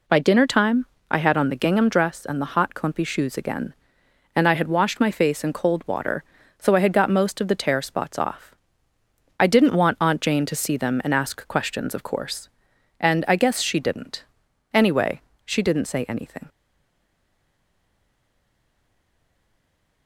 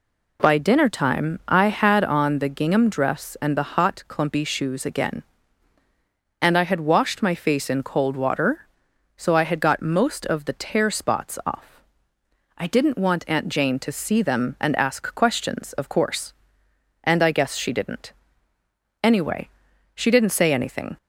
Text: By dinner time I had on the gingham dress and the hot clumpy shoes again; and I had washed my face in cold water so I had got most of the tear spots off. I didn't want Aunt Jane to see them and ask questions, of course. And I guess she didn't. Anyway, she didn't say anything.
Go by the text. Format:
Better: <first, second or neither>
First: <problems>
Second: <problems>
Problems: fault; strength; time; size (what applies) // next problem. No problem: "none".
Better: second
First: pauses between "time" and "I"; slight; at 0.8 s; 0.24 s long // stays silent after the last word; strong; from 16.4 s on; 3.6 s long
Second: none